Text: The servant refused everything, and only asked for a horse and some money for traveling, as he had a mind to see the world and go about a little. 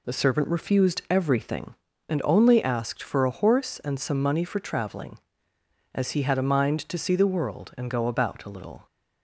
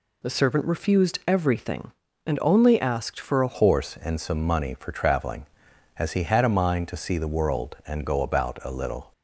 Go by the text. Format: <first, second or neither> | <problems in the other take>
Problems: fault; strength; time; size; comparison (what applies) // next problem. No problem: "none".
first | changes voice at "horse"; from 3.5 s on; 5.6 s long